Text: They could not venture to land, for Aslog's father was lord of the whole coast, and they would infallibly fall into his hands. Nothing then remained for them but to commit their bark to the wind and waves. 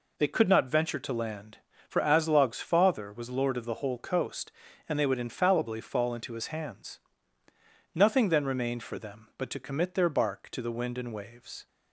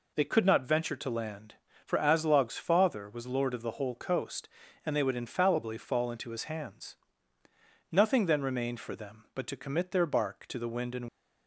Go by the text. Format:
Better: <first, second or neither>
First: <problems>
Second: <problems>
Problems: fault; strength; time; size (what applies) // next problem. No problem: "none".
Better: first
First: none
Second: stops before "waves"; at 11.0 s